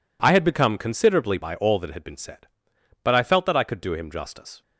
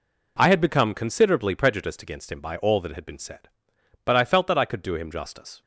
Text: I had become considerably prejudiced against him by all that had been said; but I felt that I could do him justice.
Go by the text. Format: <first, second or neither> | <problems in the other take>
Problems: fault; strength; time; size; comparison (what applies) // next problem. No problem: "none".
second | skips "prejudiced against him"; at 1.3 s